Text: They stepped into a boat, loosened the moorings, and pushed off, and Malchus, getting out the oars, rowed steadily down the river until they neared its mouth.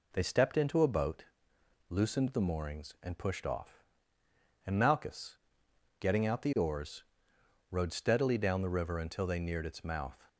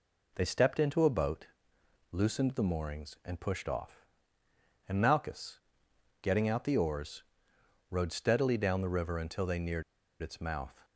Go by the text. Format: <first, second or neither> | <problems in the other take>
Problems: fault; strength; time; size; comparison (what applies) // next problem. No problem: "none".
first | pauses between "neared" and "its"; at 9.8 s; 0.39 s long